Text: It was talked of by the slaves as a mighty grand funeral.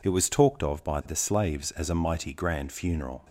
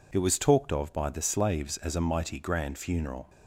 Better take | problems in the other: neither | none

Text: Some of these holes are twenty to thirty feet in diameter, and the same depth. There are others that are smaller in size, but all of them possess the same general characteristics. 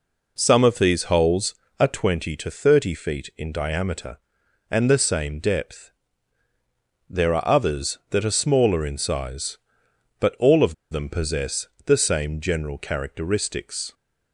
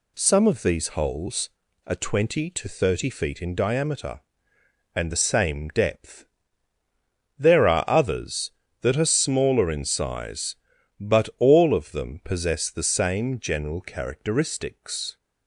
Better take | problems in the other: second | pauses between "of" and "them"; slight; at 10.7 s; 0.16 s long // pauses between "possess" and "the"; slight; at 11.6 s; 0.20 s long

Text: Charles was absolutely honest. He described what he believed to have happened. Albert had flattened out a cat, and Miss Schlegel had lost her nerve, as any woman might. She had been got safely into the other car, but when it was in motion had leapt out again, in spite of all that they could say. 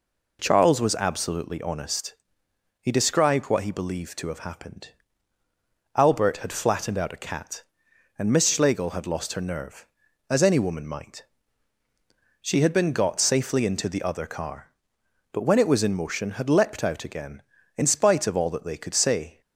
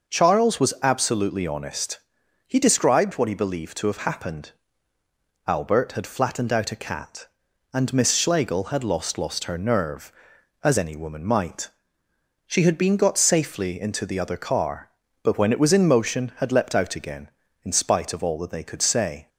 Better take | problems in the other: first | starts louder than the rest; noticeable; until 1.1 s; 6 dB // says "lost" twice; at 9.1 s

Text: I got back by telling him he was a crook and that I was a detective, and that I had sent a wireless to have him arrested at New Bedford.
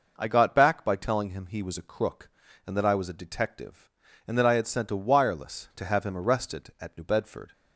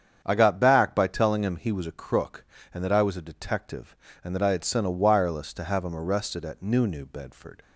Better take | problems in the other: first | starts louder than the rest; strong; until 1.2 s; 8 dB // says "New" twice; at 6.8 s

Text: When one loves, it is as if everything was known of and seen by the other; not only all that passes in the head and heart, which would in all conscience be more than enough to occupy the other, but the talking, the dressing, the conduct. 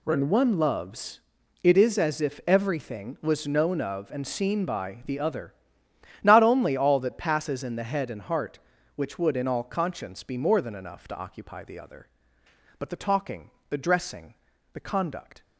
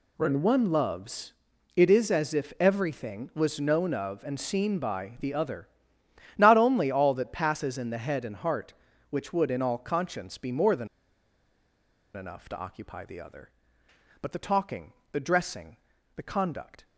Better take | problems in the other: first | pauses between "than" and "enough"; strong; at 10.8 s; 1.2 s long

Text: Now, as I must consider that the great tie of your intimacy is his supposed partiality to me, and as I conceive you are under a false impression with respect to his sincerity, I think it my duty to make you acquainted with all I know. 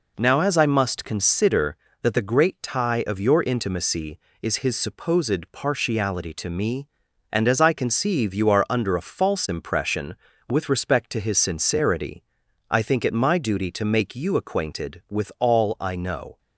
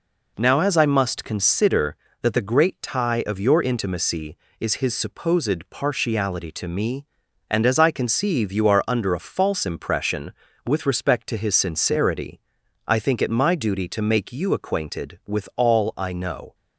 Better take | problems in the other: neither | none

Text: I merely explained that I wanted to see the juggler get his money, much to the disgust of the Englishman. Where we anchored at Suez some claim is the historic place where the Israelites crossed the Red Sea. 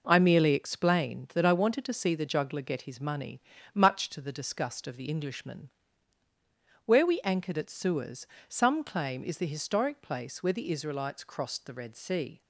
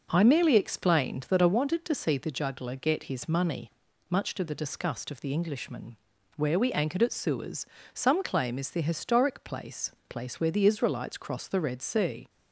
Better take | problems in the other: first | pauses between "Suez" and "some"; slight; at 7.6 s; 0.30 s long; slight in the first // says "place" twice; at 10.0 s

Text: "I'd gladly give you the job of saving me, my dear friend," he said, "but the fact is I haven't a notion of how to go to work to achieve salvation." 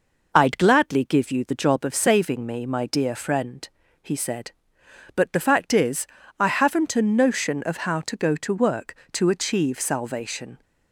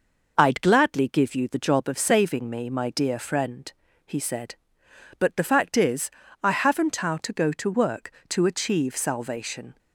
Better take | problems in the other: first | pauses between "is" and "I"; slight; at 6.1 s; 0.32 s long; slight in the first // skips "a notion of"; at 6.9 s

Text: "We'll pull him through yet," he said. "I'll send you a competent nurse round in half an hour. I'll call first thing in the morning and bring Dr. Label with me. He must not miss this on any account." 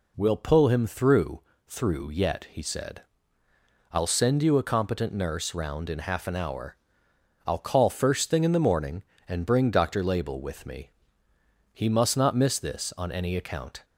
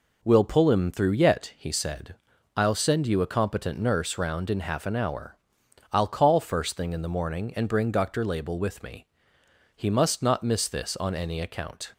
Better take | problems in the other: second | says "through" twice; at 1.6 s

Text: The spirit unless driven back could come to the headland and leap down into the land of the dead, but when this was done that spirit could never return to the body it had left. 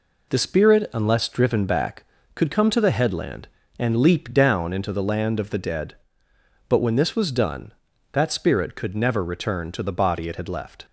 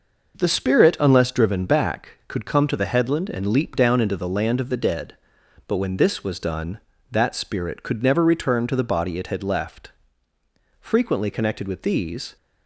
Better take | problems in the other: first | goes on to say "Frequently connected with these"; from 10.8 s on; 1.5 s long

